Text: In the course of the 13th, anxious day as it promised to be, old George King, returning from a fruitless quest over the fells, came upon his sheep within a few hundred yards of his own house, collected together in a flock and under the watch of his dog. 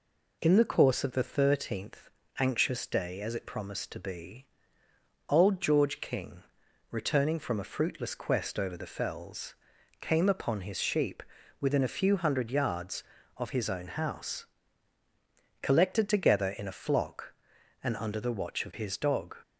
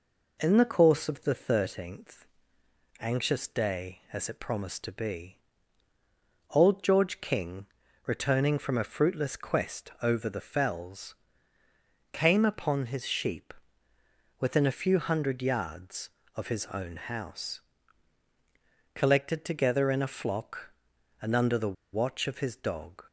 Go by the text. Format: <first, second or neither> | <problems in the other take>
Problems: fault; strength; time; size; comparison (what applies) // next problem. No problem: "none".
first | pauses between "sheep" and "within"; noticeable; at 13.5 s; 0.86 s long; slight in the first // pauses between "the" and "watch"; slight; at 21.7 s; 0.18 s long